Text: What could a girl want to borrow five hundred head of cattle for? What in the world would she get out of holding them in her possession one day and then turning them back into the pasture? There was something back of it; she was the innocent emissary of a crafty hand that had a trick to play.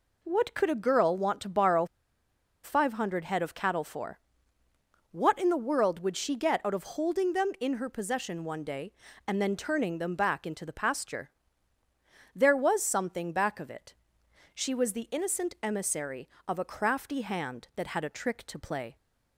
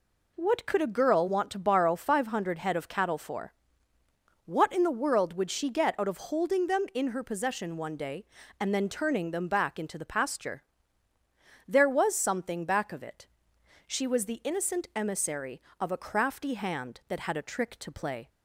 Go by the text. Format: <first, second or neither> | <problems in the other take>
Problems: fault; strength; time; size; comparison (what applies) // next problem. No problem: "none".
second | pauses between "borrow" and "five"; noticeable; at 1.8 s; 0.77 s long